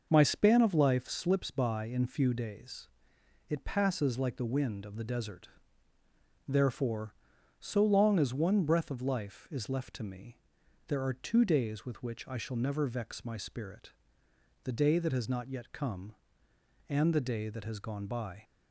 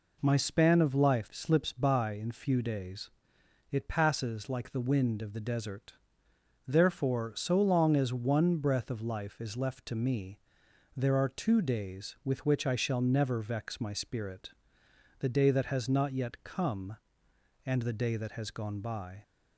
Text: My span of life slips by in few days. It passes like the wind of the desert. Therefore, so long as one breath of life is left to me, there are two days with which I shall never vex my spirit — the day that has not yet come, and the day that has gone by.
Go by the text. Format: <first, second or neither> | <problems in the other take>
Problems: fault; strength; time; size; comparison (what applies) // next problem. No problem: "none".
neither | none